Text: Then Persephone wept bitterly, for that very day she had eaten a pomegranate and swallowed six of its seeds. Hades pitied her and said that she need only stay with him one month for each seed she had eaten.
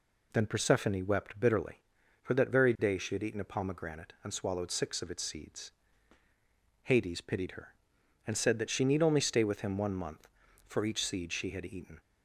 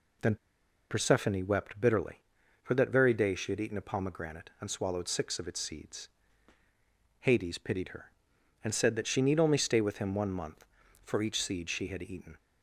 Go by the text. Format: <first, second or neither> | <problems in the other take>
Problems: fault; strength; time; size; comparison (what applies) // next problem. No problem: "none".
first | pauses between "Then" and "Persephone"; noticeable; at 0.3 s; 0.54 s long